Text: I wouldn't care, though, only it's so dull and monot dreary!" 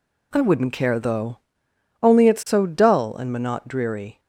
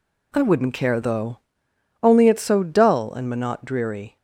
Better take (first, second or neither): neither